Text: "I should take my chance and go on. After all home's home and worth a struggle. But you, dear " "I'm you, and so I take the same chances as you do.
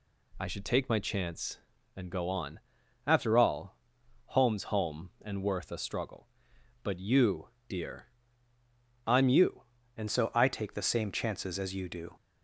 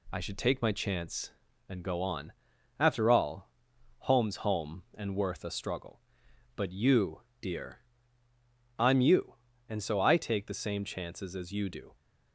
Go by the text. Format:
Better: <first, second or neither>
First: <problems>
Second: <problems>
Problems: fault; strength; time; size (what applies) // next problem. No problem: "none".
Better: second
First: pauses between "all" and "home's"; noticeable; at 3.7 s; 0.50 s long // changes voice at "so"; from 10.0 s on; 2.1 s long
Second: pauses between "all" and "home's"; noticeable; at 3.4 s; 0.50 s long